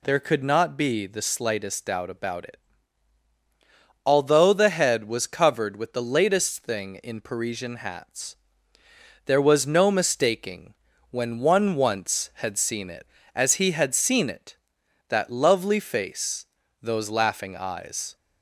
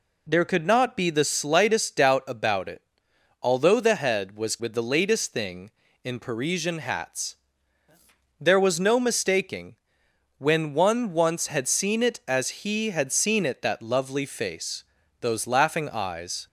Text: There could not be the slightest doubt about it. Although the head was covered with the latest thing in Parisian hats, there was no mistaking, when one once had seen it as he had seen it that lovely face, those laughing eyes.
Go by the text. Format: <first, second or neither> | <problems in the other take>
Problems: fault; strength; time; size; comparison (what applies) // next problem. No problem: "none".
first | skips "covered"; at 4.5 s